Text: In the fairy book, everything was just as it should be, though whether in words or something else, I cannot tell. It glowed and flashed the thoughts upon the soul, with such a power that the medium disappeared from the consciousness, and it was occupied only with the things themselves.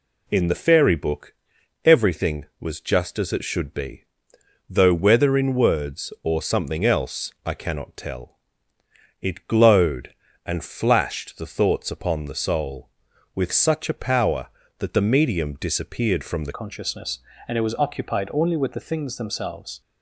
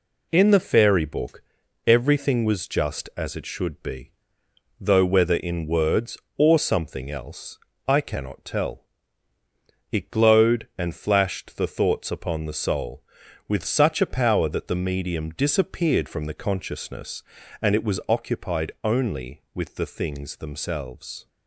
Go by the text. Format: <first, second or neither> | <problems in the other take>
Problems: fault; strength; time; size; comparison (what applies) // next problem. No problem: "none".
second | changes voice at "consciousness"; from 16.5 s on; 3.3 s long